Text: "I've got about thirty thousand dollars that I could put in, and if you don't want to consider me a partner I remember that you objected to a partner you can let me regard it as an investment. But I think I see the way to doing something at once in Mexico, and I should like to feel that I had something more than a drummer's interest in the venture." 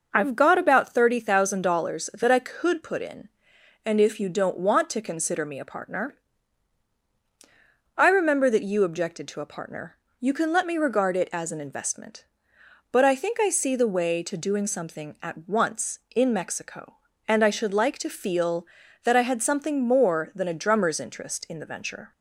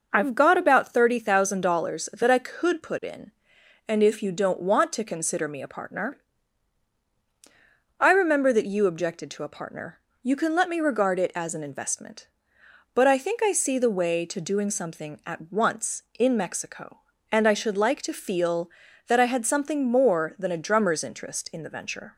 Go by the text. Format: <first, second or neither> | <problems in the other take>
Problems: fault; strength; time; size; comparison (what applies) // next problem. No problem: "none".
neither | pauses between "partner" and "I"; strong; the same in both // pauses between "partner" and "you"; slight; the same in both